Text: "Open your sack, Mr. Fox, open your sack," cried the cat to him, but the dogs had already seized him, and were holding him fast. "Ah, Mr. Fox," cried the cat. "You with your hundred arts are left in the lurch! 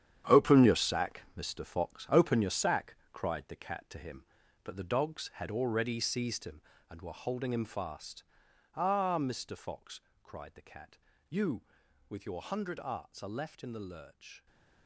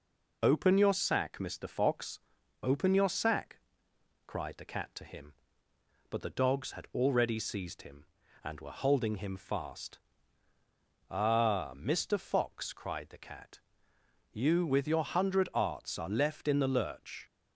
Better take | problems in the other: second | gets quieter; strong; throughout; 12 dB

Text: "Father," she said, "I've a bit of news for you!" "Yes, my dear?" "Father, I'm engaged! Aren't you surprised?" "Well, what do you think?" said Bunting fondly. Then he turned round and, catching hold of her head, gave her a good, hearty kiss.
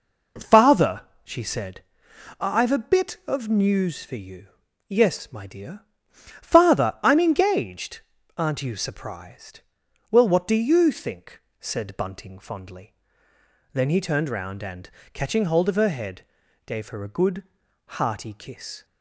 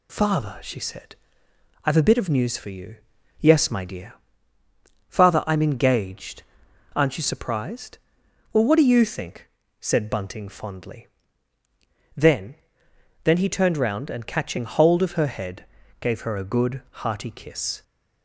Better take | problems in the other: first | says "Then" twice; at 13.2 s

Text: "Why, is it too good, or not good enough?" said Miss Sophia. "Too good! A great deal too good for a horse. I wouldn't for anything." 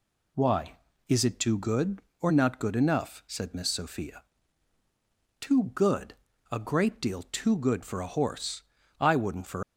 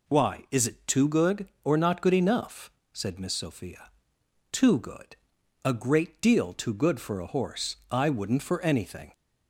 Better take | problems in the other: second | stops before "anything"; at 9.6 s

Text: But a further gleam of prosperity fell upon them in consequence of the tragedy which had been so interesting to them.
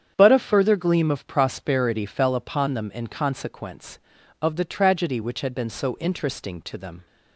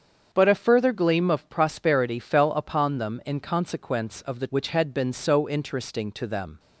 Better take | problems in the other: first | starts louder than the rest; strong; until 1.3 s; 7.5 dB; strong in the first // skips "tragedy"; at 4.4 s

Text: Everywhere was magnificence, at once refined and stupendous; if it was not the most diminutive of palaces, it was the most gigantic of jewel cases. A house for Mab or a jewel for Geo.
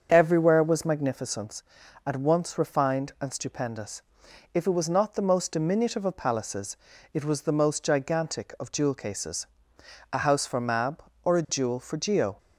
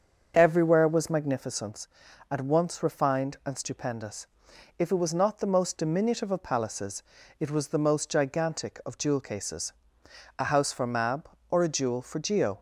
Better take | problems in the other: neither | starts louder than the rest; the same in both

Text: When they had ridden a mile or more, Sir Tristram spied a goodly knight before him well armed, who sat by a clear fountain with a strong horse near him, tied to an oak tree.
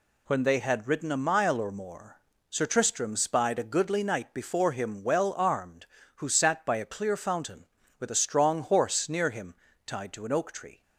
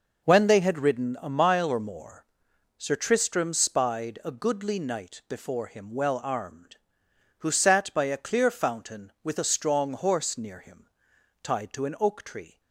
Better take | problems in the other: neither | none

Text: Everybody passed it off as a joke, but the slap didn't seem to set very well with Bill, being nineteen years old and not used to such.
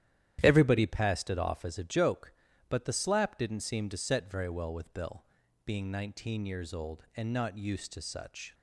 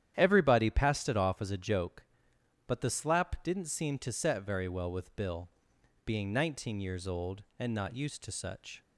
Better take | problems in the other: neither | starts louder than the rest; strong; the same in both

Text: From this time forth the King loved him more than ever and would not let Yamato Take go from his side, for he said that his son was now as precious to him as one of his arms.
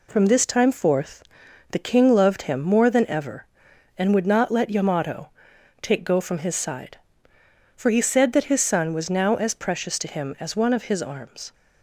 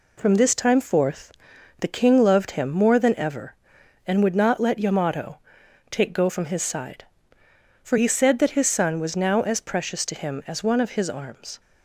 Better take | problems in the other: neither | pauses between "forth" and "the"; noticeable; the same in both // pauses between "Yamato" and "Take"; noticeable; the same in both

